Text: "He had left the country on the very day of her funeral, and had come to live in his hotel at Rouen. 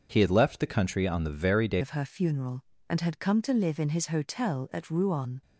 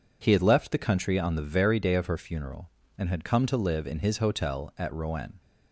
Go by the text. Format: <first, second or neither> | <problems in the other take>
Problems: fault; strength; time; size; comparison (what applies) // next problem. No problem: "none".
second | starts louder than the rest; until 1.1 s; 6.5 dB // changes voice at "of"; from 1.8 s on; 3.6 s long